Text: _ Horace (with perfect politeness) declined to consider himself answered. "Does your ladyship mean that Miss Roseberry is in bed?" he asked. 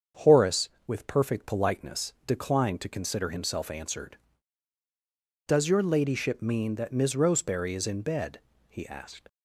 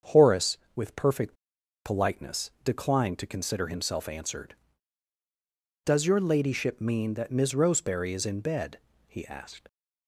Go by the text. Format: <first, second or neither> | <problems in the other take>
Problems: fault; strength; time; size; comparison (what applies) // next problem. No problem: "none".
first | starts louder than the rest; strong; until 1.2 s; 7.5 dB; strong in the first // pauses between "perfect" and "politeness"; noticeable; at 1.3 s; 0.51 s long